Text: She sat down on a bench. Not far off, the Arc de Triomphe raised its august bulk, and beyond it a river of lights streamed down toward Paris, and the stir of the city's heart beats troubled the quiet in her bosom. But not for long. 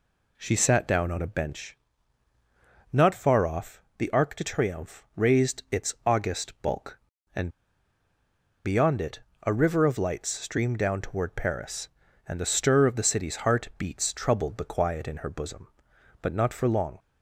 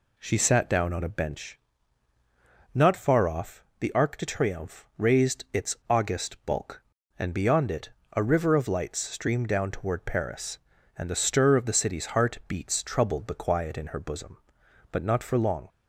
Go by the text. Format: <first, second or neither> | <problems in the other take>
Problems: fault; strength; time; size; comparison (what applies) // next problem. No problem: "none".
second | pauses between "and" and "beyond"; at 7.4 s; 1.1 s long // pauses between "it" and "a"; slight; at 9.2 s; 0.22 s long; slight in the second